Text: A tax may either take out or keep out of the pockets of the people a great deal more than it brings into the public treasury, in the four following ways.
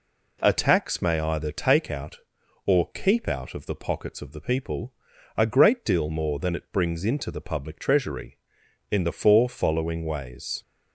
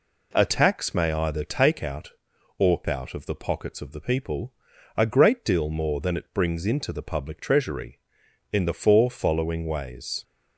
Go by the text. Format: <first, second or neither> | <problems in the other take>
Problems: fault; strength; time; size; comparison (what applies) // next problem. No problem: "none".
first | skips "keep"; at 2.8 s // pauses between "people" and "a"; at 4.5 s; 0.42 s long; also in the first